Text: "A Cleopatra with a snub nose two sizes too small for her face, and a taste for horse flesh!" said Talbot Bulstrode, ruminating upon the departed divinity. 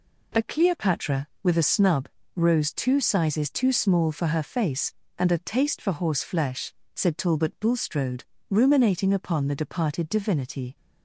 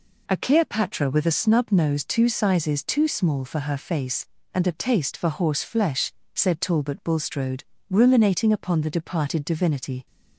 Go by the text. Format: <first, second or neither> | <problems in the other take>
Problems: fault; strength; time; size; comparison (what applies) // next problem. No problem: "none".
second | says "rose" for "nose"; at 2.3 s